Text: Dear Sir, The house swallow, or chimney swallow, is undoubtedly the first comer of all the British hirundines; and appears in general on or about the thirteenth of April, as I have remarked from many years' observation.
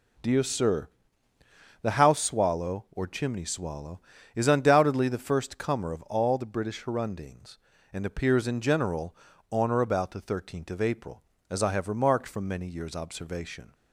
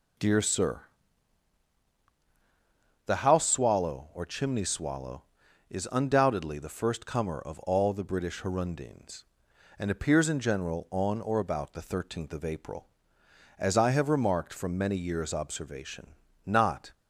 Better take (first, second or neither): first